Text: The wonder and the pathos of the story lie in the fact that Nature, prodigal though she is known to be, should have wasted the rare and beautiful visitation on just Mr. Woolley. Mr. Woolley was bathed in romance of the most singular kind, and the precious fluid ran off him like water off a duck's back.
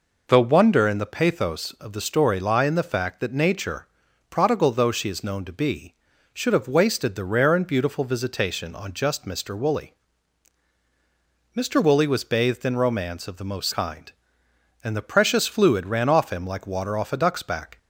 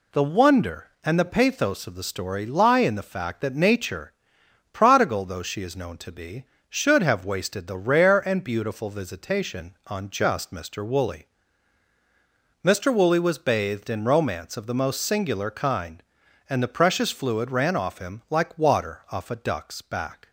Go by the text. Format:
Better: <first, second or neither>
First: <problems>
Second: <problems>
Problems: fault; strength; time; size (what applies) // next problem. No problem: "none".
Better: second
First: skips "singular"; at 13.7 s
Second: none